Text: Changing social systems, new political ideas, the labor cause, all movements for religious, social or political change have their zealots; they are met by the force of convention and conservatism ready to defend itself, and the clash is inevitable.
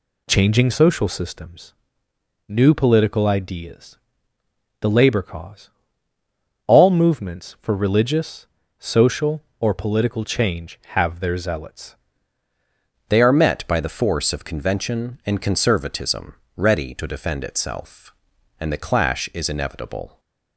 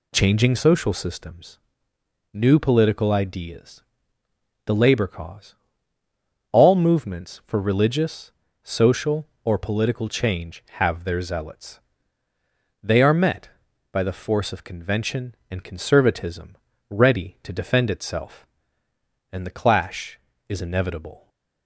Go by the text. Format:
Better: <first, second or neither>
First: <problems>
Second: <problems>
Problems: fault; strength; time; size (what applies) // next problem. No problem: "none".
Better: second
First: changes voice at "they"; from 13.0 s on; 7.1 s long // pauses between "conservatism" and "ready"; slight; at 16.3 s; 0.24 s long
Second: pauses between "conservatism" and "ready"; slight; at 16.5 s; 0.32 s long